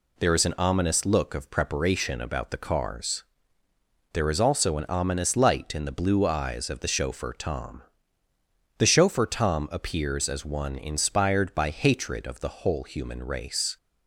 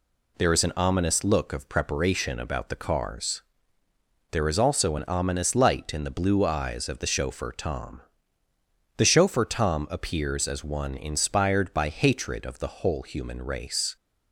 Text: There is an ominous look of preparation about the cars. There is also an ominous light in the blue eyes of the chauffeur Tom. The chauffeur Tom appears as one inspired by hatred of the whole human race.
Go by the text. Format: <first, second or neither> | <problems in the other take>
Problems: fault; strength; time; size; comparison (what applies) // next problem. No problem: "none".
neither | none